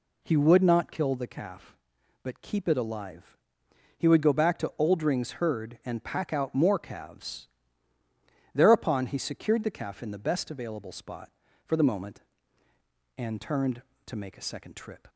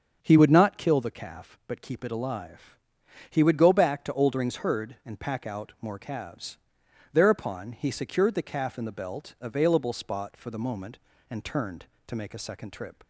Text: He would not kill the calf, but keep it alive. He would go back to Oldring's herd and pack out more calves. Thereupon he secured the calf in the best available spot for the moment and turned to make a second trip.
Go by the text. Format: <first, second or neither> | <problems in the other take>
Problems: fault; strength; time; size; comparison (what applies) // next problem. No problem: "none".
first | starts louder than the rest; strong; until 1.2 s; 7 dB // says "belt" for "best"; at 8.9 s